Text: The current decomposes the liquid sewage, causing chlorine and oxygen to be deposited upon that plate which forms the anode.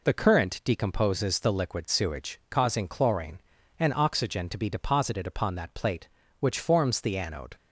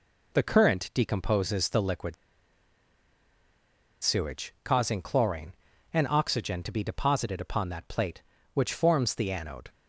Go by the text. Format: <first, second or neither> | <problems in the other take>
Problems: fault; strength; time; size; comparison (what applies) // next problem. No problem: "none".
first | pauses between "liquid" and "sewage"; strong; at 2.1 s; 1.8 s long